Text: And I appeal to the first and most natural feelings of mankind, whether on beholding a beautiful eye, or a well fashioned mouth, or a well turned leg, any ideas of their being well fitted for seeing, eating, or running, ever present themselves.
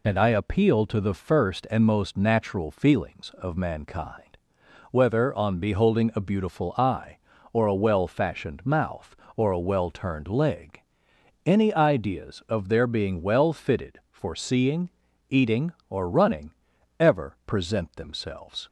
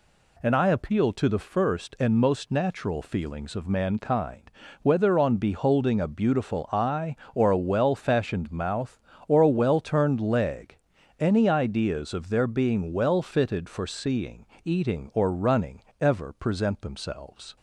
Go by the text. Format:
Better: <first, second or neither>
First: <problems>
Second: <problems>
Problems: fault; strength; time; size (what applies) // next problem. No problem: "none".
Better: second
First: loses the start of "And"; at 0.0 s; 25 ms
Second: none